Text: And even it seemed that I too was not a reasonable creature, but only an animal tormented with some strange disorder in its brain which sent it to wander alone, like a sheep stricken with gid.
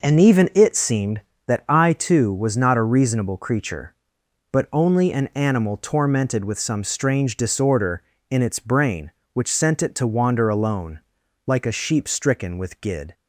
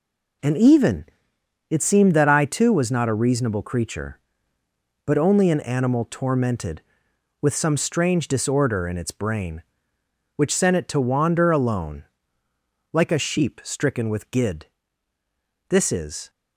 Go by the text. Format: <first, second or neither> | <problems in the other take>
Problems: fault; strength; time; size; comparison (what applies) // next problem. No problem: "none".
first | pauses between "even" and "it"; noticeable; at 1.0 s; 0.64 s long // goes on to say "This is"; from 15.6 s on; 0.60 s long